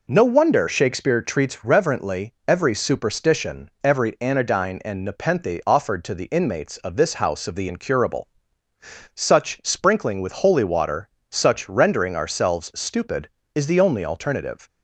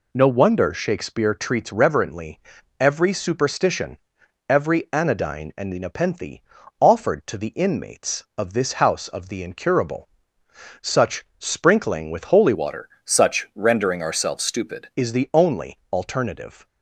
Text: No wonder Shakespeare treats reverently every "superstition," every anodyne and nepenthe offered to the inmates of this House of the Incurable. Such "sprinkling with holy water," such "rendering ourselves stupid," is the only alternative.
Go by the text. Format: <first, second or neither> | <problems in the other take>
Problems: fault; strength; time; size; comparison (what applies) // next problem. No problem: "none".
first | pauses between "reverently" and "every"; at 2.4 s; 0.40 s long // pauses between "nepenthe" and "offered"; at 6.4 s; 0.40 s long // pauses between "Such" and "sprinkling"; slight; at 11.2 s; 0.16 s long // changes voice from "water" to "stupid"; from 12.5 to 14.8 s; 2.3 s long